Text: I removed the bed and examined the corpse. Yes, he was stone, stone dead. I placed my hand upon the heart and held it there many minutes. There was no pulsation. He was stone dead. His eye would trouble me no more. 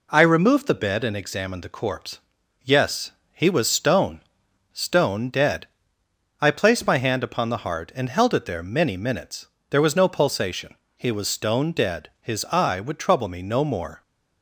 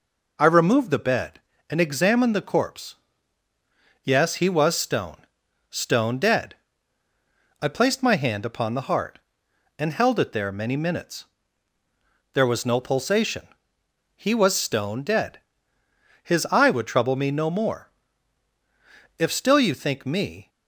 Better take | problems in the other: first | goes on to say "If still you think me"; noticeable; from 19.1 s on; 1.3 s long

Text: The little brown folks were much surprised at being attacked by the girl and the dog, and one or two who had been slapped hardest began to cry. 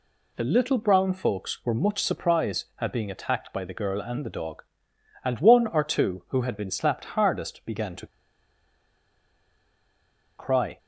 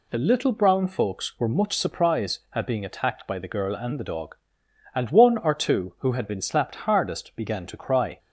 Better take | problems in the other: second | pauses between "to" and "cry"; strong; at 8.0 s; 2.3 s long

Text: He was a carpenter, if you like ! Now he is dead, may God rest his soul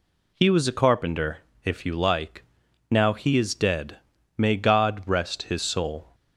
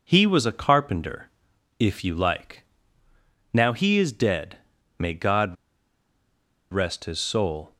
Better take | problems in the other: first | pauses between "God" and "rest"; at 5.5 s; 1.1 s long

